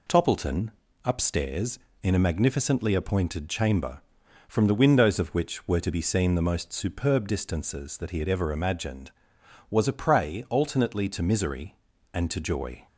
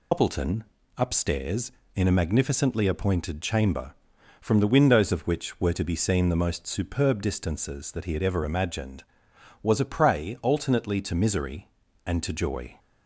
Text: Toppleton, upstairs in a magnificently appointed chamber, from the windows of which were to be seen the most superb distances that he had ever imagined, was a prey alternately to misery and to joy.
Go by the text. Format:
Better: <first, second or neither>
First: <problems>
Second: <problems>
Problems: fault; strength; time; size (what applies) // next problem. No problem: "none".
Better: first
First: none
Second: loses the start of "Toppleton"; at 0.1 s; 110 ms